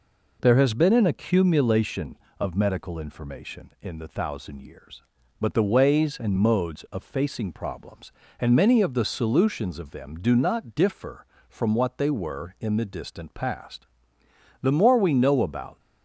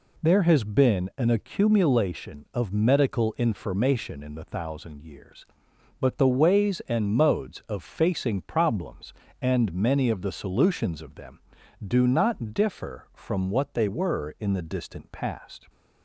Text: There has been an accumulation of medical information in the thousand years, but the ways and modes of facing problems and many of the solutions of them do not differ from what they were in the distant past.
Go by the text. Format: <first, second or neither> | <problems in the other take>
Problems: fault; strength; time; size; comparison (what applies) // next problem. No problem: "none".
second | goes on to say "The more we know about"; noticeable; from 14.6 s on; 1.1 s long